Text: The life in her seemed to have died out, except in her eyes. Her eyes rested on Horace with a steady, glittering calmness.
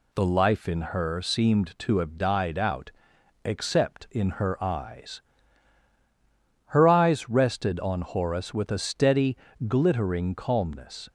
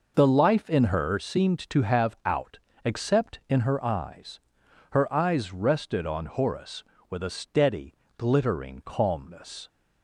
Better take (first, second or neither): first